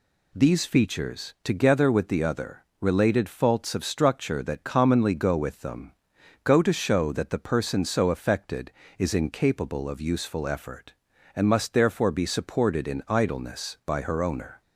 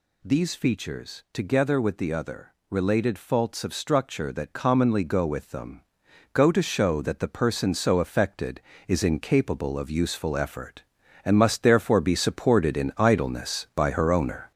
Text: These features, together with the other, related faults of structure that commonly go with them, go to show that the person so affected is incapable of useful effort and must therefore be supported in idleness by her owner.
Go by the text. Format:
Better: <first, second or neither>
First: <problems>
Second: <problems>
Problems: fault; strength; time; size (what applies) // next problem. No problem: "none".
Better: first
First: none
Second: gets louder; noticeable; throughout; 6 dB